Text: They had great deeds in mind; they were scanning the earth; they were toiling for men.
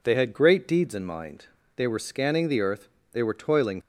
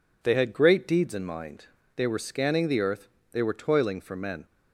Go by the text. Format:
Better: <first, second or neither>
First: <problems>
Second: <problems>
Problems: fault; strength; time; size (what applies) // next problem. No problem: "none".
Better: second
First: stops before "for men"; at 3.8 s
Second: none